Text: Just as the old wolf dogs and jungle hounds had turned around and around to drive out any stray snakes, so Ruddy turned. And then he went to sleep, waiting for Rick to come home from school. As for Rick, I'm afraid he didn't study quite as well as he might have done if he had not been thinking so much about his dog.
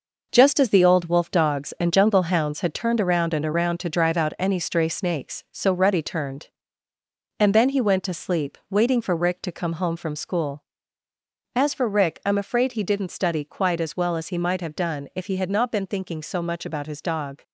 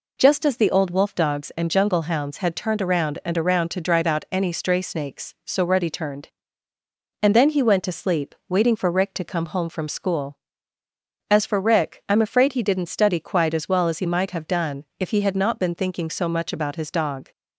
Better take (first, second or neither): second